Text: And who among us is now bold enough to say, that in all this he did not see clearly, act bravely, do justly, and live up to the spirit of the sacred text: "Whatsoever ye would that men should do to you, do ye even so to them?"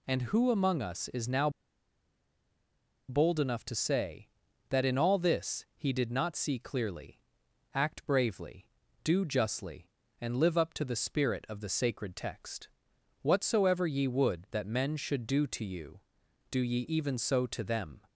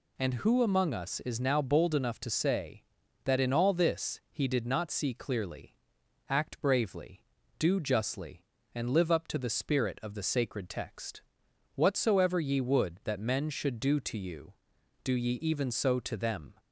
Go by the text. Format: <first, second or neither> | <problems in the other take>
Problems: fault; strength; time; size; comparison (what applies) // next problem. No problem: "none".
second | pauses between "now" and "bold"; strong; at 1.4 s; 1.5 s long